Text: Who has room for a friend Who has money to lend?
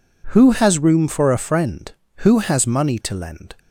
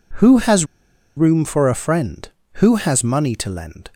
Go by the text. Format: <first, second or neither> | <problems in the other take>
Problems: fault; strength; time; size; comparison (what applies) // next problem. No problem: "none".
first | pauses between "has" and "room"; noticeable; at 0.6 s; 0.50 s long